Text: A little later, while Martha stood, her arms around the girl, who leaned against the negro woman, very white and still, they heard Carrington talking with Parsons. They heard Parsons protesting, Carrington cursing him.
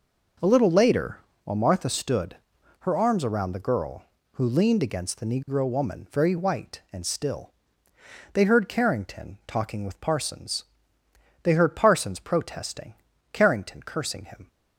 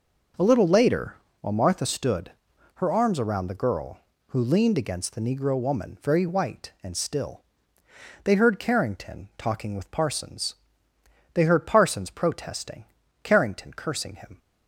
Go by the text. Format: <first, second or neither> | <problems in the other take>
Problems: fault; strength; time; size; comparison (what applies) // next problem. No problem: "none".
neither | none